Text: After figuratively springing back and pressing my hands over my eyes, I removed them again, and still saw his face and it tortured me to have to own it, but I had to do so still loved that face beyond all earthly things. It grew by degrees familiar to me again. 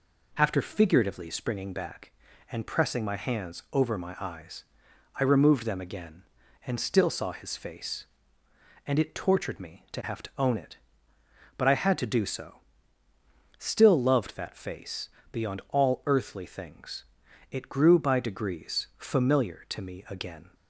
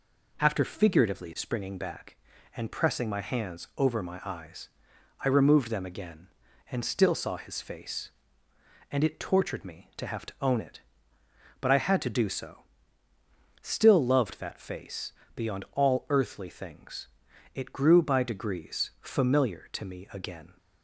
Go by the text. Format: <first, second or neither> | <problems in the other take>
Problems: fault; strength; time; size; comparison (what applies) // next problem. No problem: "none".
neither | pauses between "so" and "still"; the same in both // pauses between "face" and "beyond"; slight; the same in both